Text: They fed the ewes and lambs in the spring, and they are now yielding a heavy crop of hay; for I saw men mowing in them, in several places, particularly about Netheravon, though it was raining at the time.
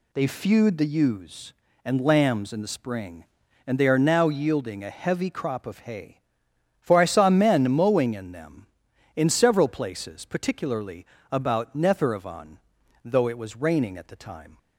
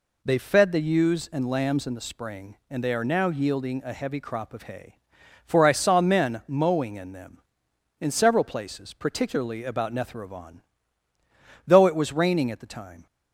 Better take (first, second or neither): second